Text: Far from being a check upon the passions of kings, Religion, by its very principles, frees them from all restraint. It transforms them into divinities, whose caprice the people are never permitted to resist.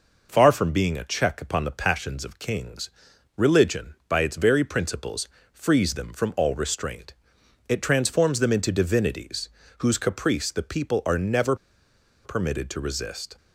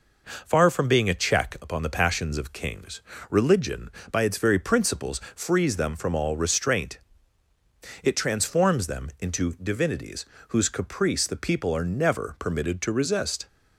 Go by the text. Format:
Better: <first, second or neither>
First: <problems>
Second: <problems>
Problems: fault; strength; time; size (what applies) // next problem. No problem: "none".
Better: second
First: pauses between "never" and "permitted"; noticeable; at 11.5 s; 0.68 s long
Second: none